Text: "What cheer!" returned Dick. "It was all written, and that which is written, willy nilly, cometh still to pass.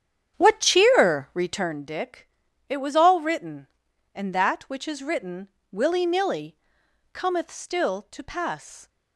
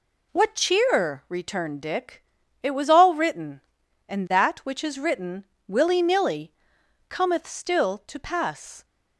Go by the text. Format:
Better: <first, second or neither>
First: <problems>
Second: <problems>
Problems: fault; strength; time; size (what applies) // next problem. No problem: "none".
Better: second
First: starts louder than the rest; strong; until 1.8 s; 9 dB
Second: none